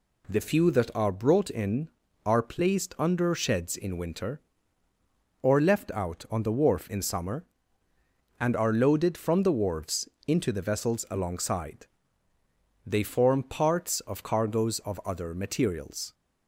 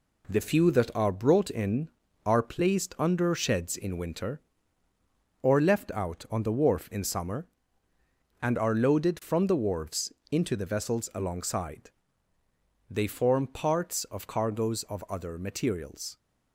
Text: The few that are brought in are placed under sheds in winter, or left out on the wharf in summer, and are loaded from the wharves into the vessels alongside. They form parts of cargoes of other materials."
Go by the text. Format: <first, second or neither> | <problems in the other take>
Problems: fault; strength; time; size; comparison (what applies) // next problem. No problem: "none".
first | gets quieter; noticeable; throughout; 5.5 dB // pauses between "wharves" and "into"; slight; at 10.1 s; 0.18 s long; slight in the first